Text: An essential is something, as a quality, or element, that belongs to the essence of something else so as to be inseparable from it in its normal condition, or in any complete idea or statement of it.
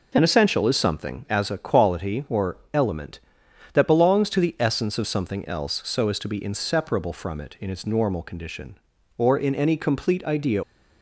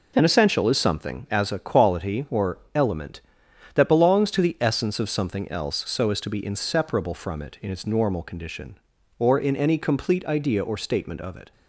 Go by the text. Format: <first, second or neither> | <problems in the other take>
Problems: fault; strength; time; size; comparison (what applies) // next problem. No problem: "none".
second | stops before "or statement of it"; at 10.6 s